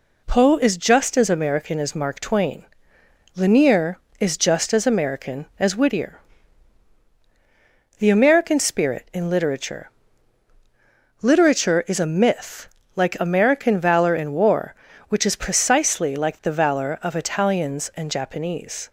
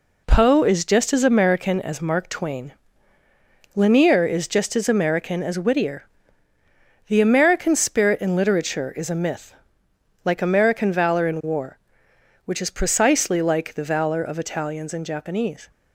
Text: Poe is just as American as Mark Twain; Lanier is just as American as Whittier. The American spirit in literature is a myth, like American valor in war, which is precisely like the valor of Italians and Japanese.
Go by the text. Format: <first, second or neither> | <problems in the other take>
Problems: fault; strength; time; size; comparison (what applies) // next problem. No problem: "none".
second | says "literature" twice; at 11.2 s